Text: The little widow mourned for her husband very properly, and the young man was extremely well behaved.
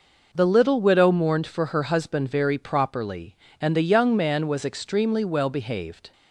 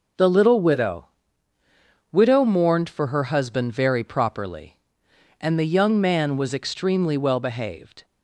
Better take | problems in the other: first | says "widow" twice; at 2.1 s

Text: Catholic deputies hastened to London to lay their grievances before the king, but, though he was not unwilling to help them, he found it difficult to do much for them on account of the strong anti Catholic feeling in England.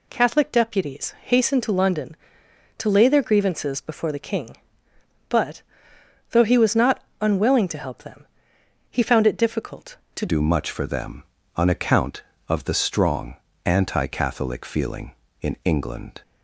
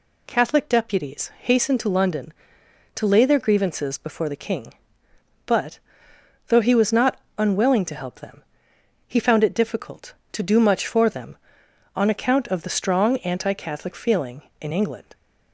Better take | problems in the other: second | pauses between "not" and "unwilling"; slight; at 7.0 s; 0.18 s long; slight in the second // changes voice at "do"; from 10.2 s on; 6.0 s long // pauses between "strong" and "anti"; slight; at 13.3 s; 0.28 s long

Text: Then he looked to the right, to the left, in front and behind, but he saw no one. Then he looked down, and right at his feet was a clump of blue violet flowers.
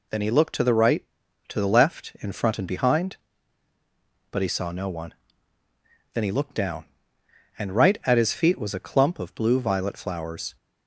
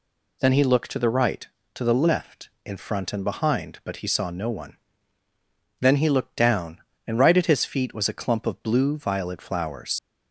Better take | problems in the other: first | leaves "flowers" unfinished; at 9.9 s; 80 ms

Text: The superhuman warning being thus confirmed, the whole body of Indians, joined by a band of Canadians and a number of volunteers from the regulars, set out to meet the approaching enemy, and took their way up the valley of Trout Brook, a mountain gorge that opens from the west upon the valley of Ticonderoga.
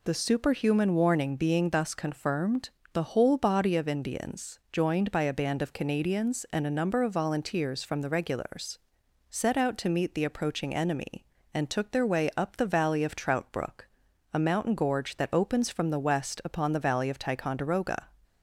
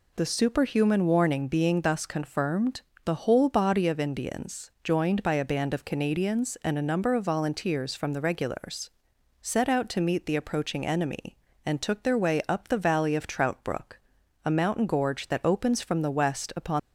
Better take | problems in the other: first | stops before "the valley of Ticonderoga"; at 16.7 s

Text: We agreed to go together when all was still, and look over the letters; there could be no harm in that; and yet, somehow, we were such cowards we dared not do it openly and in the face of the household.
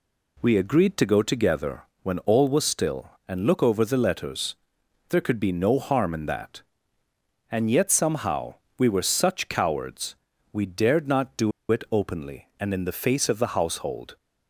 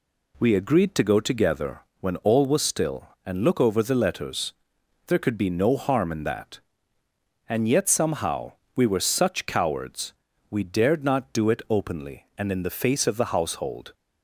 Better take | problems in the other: second | pauses between "together" and "when"; slight; at 1.8 s; 0.22 s long; slight in the second // pauses between "cowards" and "we"; at 10.1 s; 0.38 s long; also in the second // pauses between "do" and "it"; slight; at 11.5 s; 0.20 s long

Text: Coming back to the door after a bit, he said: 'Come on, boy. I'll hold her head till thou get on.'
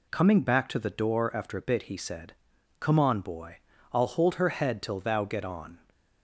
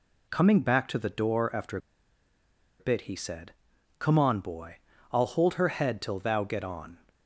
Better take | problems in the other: first | pauses between "after" and "a"; at 1.7 s; 1.0 s long

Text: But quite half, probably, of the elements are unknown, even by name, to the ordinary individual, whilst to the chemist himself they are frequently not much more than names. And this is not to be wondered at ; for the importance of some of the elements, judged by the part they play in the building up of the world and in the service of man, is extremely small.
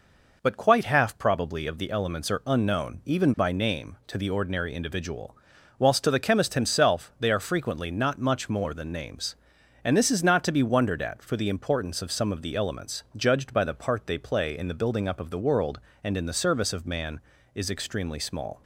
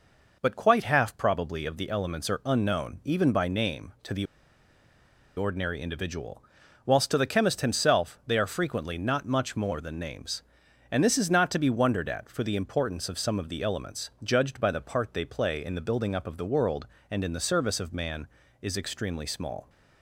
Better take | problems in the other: first | pauses between "the" and "ordinary"; at 4.2 s; 1.1 s long

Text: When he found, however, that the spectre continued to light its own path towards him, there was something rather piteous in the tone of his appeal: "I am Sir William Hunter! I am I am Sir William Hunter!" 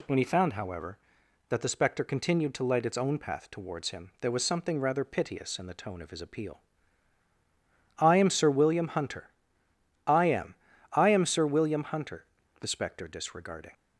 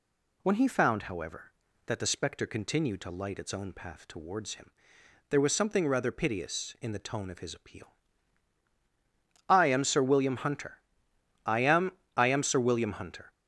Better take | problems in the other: second | pauses between "am" and "I"; at 10.5 s; 0.38 s long; slight in the second // goes on to say "The spectre disregarding"; noticeable; from 12.5 s on; 1.1 s long

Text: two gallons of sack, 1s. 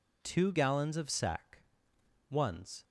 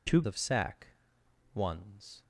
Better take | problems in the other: first | skips "gallons"; at 0.2 s

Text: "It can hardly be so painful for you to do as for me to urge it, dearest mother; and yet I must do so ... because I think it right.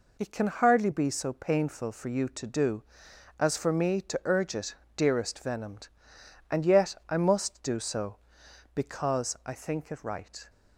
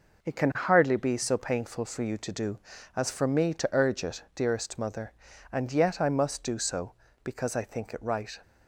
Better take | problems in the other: second | says "venomed" for "mother"; at 5.3 s

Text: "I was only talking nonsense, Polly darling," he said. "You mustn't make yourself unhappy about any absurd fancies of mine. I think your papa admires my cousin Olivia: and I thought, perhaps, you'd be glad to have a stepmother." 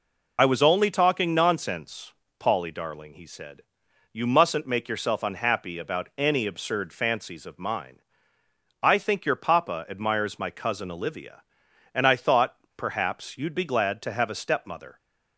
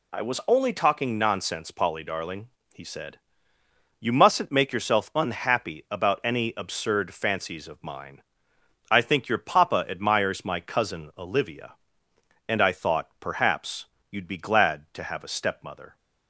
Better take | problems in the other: second | loses the start of "I"; at 0.3 s; 30 ms

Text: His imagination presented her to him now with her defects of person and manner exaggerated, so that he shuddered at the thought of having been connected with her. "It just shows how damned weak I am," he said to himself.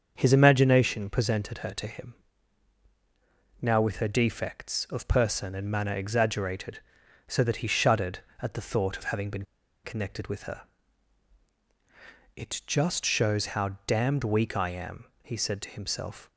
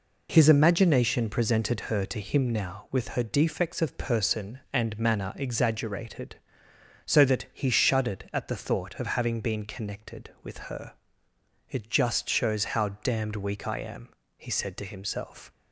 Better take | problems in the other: second | starts louder than the rest; until 1.1 s; 7 dB // pauses between "him" and "now"; strong; at 2.1 s; 1.4 s long // pauses between "been" and "connected"; at 9.4 s; 0.39 s long

